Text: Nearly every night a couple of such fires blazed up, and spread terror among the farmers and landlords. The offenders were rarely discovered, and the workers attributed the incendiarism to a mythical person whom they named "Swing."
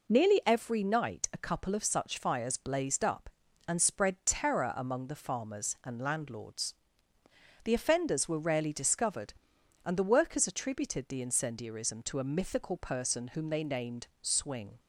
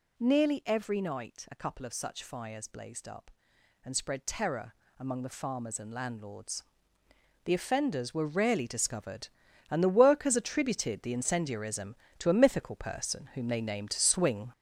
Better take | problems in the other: first | gets louder; throughout; 6.5 dB // pauses between "terror" and "among"; slight; at 4.7 s; 0.26 s long

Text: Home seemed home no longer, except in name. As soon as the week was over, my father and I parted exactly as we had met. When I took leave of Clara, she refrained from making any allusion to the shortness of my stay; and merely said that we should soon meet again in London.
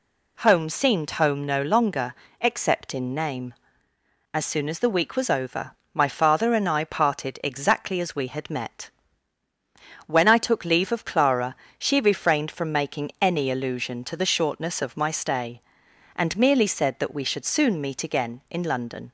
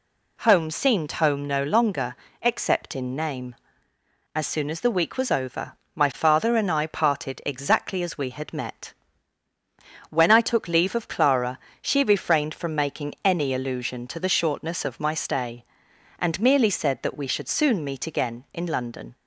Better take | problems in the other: neither | none

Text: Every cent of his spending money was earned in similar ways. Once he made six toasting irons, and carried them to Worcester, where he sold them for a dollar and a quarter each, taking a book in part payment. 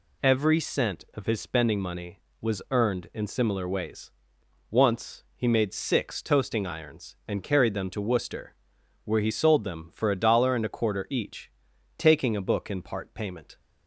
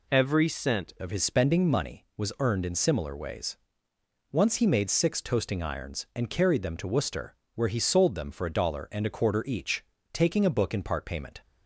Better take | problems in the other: first | changes voice at "of"; from 1.0 s on; 10.4 s long

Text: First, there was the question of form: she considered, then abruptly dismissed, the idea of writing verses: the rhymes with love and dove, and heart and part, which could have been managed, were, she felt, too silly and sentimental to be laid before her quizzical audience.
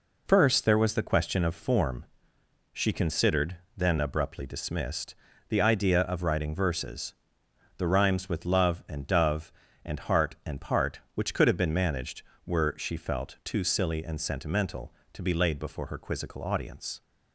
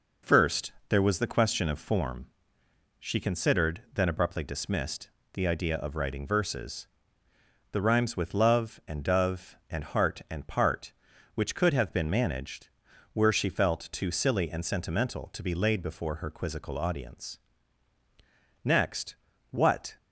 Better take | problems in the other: first | goes on to say "Next what"; from 18.6 s on; 1.3 s long

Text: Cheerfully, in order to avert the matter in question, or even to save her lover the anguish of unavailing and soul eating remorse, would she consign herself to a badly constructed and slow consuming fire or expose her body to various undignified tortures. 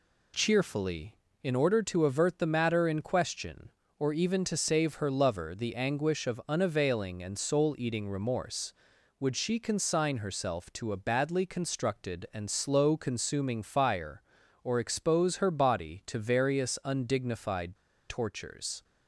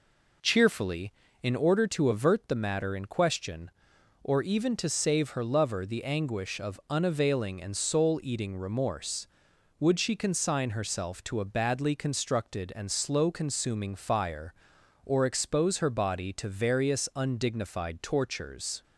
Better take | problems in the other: second | pauses between "undignified" and "tortures"; slight; at 17.7 s; 0.33 s long

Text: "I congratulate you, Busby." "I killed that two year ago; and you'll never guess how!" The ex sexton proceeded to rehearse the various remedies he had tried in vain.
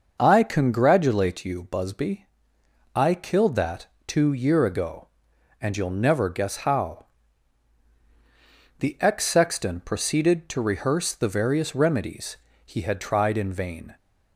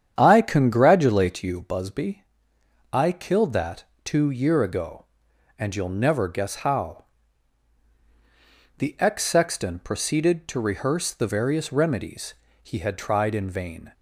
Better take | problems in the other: first | starts louder than the rest; strong; until 1.8 s; 8.5 dB // pauses between "that" and "two"; slight; at 3.8 s; 0.22 s long; slight in the first // pauses between "remedies" and "he"; slight; at 12.3 s; 0.26 s long; slight in the first

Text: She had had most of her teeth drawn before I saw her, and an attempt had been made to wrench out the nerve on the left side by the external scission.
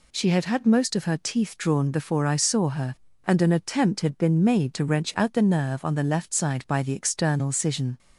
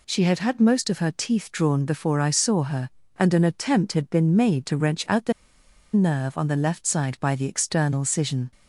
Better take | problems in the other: first | pauses between "the" and "nerve"; noticeable; at 5.3 s; 0.62 s long

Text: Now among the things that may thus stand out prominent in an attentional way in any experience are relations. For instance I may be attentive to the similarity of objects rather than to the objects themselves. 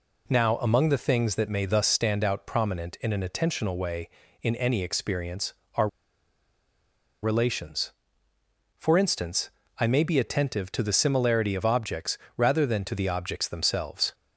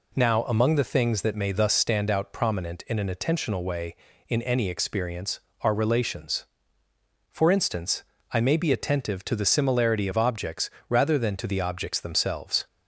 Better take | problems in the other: second | pauses between "are" and "relations"; strong; at 5.8 s; 1.3 s long // pauses between "instance" and "I"; slight; at 9.4 s; 0.32 s long; slight in the second // pauses between "objects" and "rather"; slight; at 12.1 s; 0.18 s long; slight in the second

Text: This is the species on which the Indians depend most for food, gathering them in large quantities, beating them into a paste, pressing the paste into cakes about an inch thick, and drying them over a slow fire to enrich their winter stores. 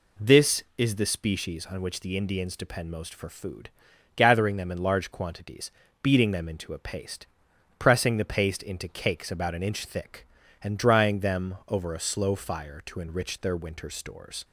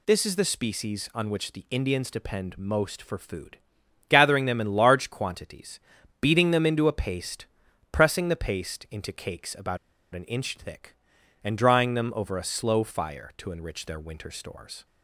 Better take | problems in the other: first | pauses between "about" and "an"; at 9.7 s; 0.37 s long

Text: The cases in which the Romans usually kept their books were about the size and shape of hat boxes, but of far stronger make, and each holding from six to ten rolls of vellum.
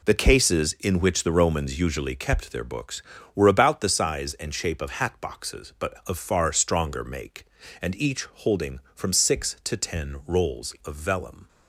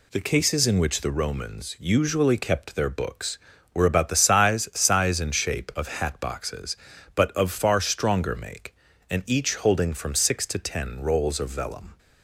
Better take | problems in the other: first | says "size" twice; at 4.7 s

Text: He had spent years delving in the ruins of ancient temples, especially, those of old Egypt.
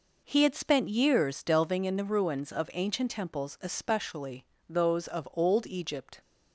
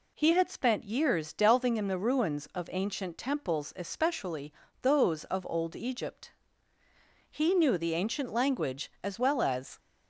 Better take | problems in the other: first | goes on to say "He knew the ancient language as well as"; strong; from 7.2 s on; 2.5 s long

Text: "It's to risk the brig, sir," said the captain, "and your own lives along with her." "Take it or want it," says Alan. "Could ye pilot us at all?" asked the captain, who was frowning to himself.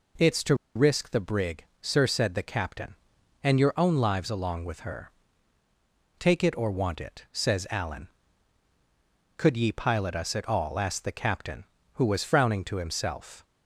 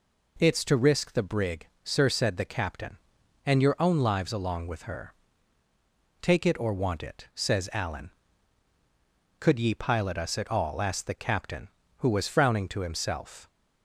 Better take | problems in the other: second | pauses between "to" and "risk"; slight; at 0.5 s; 0.21 s long

